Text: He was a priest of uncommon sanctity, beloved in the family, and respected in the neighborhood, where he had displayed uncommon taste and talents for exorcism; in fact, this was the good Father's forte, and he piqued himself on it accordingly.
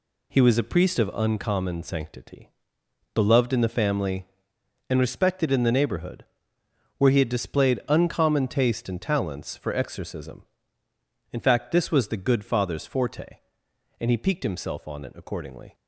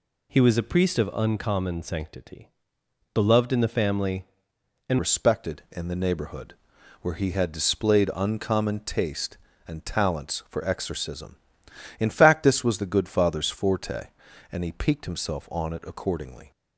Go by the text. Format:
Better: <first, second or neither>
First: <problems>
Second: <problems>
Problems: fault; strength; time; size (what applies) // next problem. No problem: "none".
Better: first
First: none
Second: changes voice at "respected"; from 4.9 s on; 11.6 s long